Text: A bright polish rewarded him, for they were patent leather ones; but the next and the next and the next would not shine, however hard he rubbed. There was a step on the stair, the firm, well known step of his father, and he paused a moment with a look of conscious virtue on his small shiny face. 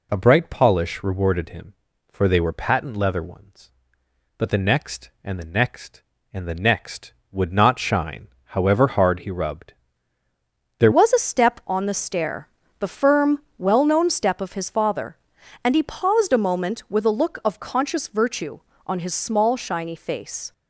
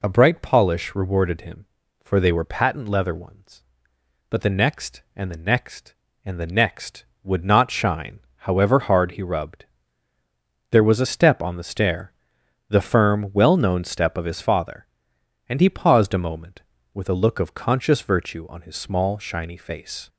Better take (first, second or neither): second